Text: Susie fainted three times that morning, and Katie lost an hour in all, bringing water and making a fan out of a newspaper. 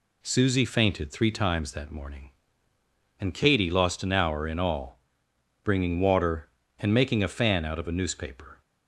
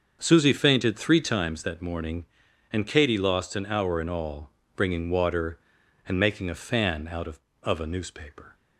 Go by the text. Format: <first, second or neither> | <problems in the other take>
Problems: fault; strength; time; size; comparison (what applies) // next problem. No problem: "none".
first | starts louder than the rest; until 1.2 s; 6.5 dB // says "of" twice; at 7.6 s